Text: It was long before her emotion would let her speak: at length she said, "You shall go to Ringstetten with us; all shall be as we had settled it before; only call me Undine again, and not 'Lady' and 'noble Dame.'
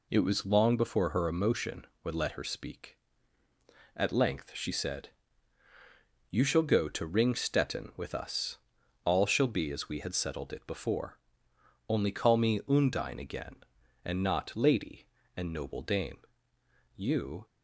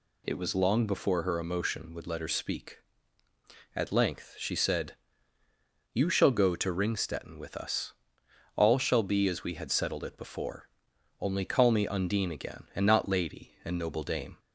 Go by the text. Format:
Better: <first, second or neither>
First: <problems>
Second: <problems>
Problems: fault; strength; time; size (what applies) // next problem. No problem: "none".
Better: second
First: goes on to say "You"; from 16.9 s on; 0.50 s long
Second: none